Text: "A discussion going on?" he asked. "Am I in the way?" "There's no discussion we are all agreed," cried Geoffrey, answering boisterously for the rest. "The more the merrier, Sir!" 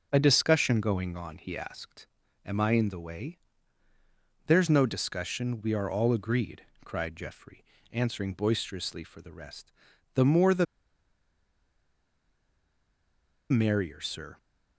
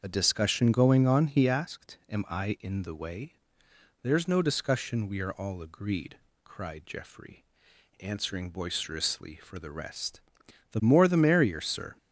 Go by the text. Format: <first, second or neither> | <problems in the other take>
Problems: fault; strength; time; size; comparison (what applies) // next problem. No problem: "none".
second | starts louder than the rest; noticeable; until 1.1 s; 6 dB; also in the second // pauses between "the" and "merrier"; strong; at 10.6 s; 2.8 s long